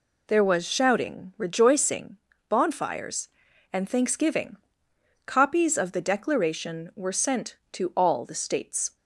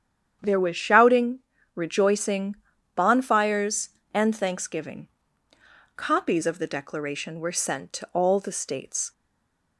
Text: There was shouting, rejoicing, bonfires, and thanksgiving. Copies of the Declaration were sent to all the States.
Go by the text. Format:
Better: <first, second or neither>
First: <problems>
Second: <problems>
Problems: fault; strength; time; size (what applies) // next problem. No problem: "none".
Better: first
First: none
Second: starts louder than the rest; strong; until 1.4 s; 9 dB // stays silent after the last word; slight; from 9.1 s on; 0.6 s long